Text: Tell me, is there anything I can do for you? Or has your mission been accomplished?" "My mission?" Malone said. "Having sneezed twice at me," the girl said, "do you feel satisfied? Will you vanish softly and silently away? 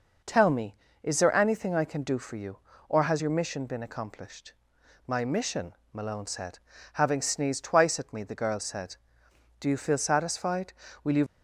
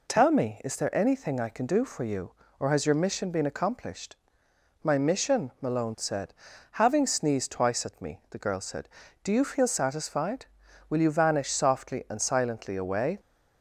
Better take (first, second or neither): second